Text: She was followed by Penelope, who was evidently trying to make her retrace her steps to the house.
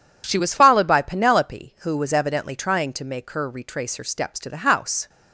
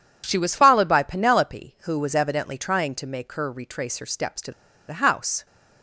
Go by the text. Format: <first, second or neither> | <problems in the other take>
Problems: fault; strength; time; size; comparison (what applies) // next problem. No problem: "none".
first | pauses between "to" and "the"; at 4.5 s; 0.37 s long